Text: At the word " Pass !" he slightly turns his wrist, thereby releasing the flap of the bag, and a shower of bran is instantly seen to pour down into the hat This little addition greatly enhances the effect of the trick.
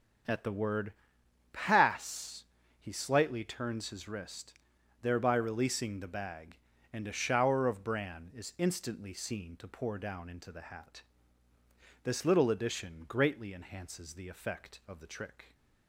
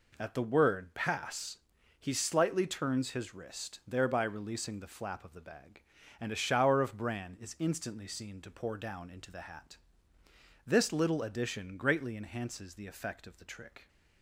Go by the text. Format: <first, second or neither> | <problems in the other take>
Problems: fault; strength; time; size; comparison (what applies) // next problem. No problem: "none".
second | skips "the flap of"; at 6.0 s // pauses between "hat" and "This"; at 11.0 s; 1.0 s long; noticeable in the second